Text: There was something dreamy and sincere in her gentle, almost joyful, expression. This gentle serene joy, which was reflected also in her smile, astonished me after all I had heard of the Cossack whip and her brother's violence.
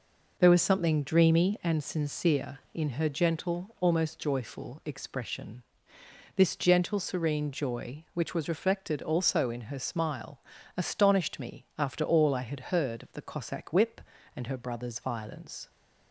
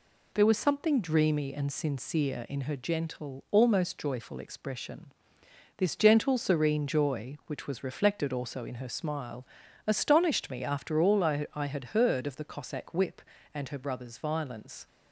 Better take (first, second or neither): first